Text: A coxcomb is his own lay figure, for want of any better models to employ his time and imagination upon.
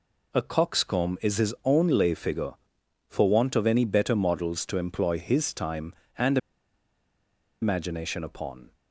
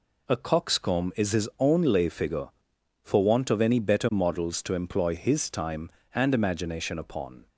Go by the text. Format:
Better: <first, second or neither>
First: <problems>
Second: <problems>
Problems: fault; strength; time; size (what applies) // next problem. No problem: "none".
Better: second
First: pauses between "and" and "imagination"; at 6.3 s; 1.2 s long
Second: none